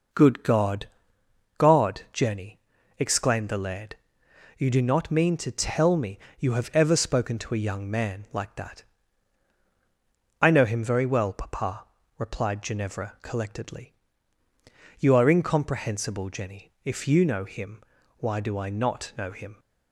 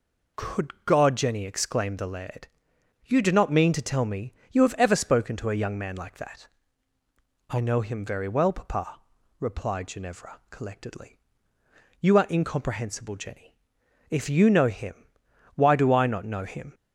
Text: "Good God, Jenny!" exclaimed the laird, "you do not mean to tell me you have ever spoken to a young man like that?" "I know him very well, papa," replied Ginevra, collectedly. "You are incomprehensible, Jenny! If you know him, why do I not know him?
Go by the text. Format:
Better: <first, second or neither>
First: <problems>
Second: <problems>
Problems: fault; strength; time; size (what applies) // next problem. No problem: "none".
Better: second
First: says "God" twice; at 1.5 s // pauses between "me" and "you"; slight; at 6.1 s; 0.18 s long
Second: pauses between "me" and "you"; slight; at 4.3 s; 0.16 s long